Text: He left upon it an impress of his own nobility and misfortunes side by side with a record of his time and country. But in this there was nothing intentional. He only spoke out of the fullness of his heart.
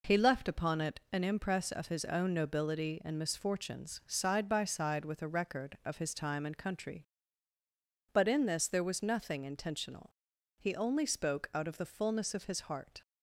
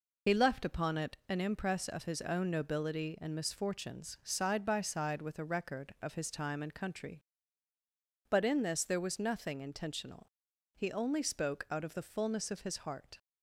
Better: first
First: none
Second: loses the start of "He"; at 0.2 s; 55 ms

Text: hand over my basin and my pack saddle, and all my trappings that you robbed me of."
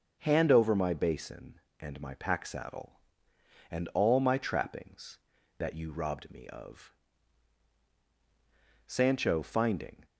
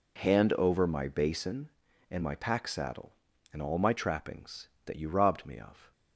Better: second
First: goes on to say "Sancho finding"; noticeable; from 8.8 s on; 1.1 s long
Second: none

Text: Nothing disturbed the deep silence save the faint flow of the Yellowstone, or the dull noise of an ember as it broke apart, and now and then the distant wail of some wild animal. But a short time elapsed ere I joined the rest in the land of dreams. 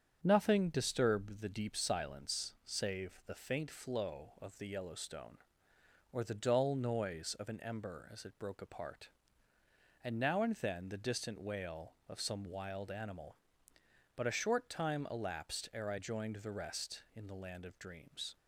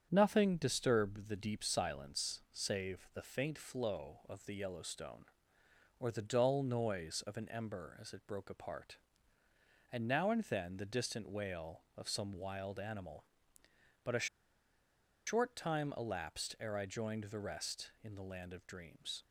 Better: first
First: starts louder than the rest; strong; until 1.2 s; 7 dB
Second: starts louder than the rest; strong; until 1.1 s; 7 dB // pauses between "a" and "short"; at 14.2 s; 1.0 s long

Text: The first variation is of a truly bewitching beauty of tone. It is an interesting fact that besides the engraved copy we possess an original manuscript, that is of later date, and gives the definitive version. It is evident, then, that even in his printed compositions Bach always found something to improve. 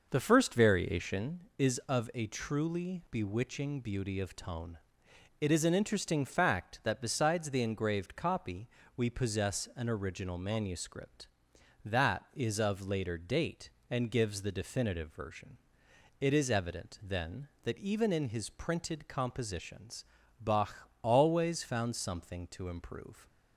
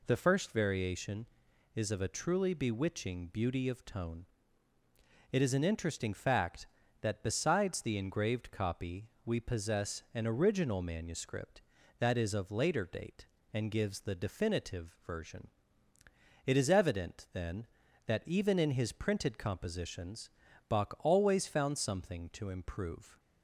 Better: second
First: starts louder than the rest; noticeable; until 1.4 s; 5.5 dB // pauses between "copy" and "we"; slight; at 8.6 s; 0.26 s long // pauses between "compositions" and "Bach"; slight; at 20.0 s; 0.34 s long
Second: pauses between "copy" and "we"; slight; at 9.0 s; 0.18 s long // pauses between "compositions" and "Bach"; at 20.2 s; 0.38 s long

